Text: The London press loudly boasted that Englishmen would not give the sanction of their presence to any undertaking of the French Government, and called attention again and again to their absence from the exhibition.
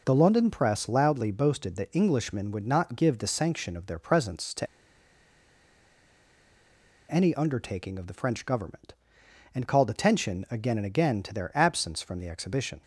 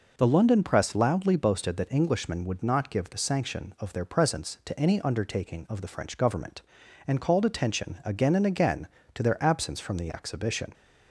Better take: second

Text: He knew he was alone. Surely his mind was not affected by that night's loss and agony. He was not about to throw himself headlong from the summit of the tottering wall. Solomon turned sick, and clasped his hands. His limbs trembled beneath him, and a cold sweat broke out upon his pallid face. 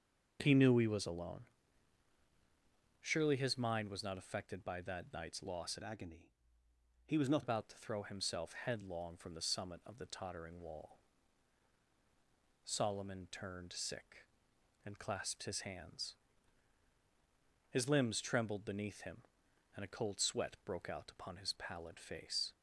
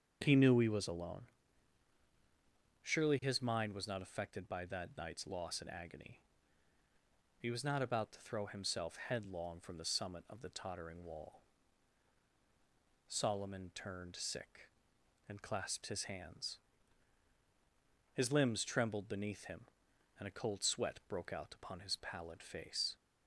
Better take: second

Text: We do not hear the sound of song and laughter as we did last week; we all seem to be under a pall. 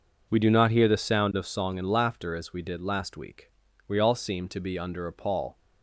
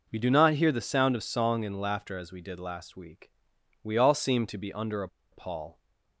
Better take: first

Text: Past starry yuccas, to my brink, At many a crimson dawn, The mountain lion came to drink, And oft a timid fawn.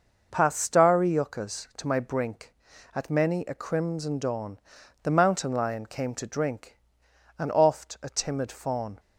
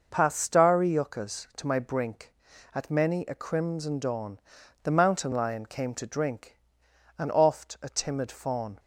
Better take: neither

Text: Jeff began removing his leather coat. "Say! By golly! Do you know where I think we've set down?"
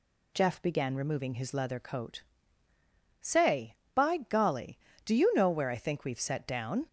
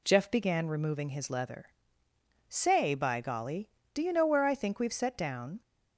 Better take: first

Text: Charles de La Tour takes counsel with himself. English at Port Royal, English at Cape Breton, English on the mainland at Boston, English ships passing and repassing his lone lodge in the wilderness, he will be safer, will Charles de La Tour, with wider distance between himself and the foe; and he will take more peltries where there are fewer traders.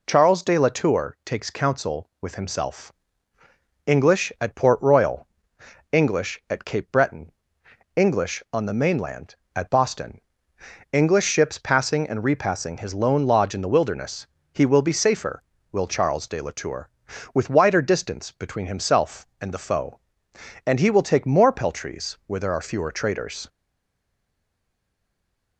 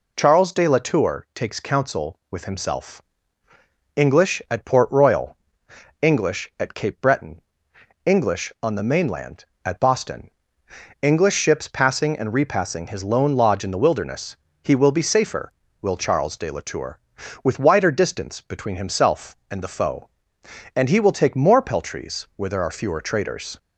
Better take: second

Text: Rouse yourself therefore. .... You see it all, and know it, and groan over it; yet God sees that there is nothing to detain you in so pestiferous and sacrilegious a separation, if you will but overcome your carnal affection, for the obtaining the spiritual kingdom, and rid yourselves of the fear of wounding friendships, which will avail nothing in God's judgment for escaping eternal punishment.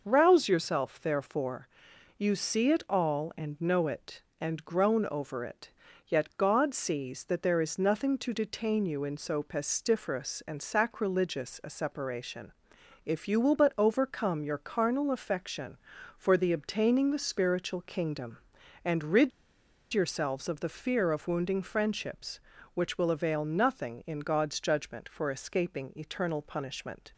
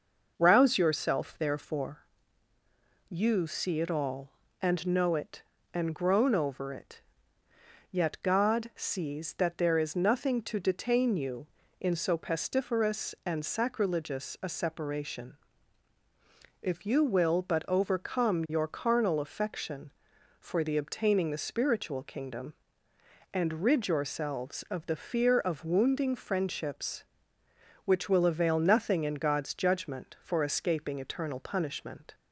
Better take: second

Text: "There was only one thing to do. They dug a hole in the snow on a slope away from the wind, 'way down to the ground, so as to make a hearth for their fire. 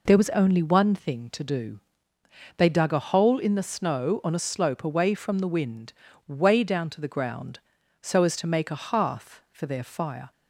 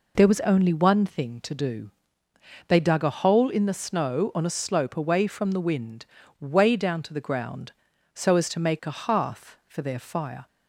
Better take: neither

